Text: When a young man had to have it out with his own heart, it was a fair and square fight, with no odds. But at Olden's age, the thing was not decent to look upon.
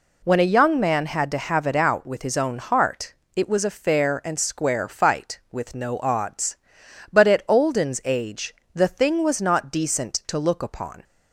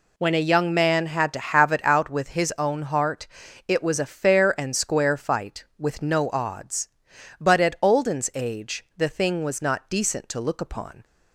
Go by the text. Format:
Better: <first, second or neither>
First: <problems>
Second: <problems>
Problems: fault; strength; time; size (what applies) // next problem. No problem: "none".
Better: neither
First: none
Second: none